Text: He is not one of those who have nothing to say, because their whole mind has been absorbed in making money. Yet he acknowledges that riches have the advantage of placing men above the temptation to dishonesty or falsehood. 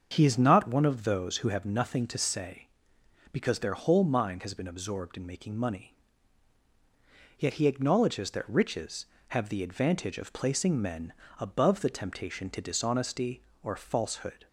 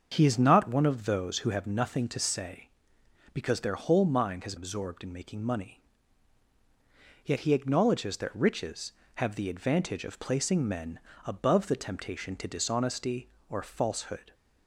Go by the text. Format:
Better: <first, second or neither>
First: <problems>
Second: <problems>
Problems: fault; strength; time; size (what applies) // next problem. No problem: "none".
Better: first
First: starts louder than the rest; until 1.1 s; 7 dB // pauses between "men" and "above"; slight; at 11.1 s; 0.26 s long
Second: starts louder than the rest; until 1.1 s; 6.5 dB // skips "been"; at 4.5 s // pauses between "men" and "above"; slight; at 10.9 s; 0.26 s long